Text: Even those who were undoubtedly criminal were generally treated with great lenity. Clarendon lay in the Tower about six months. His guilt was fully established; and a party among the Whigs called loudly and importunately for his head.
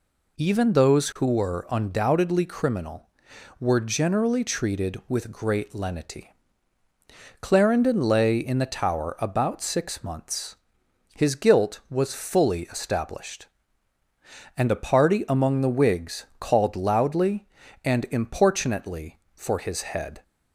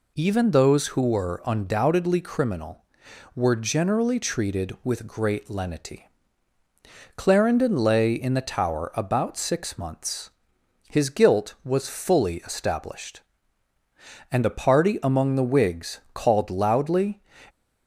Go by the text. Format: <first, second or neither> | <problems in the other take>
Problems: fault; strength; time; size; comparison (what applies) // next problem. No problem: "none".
first | stops before "and importunately for his head"; at 17.4 s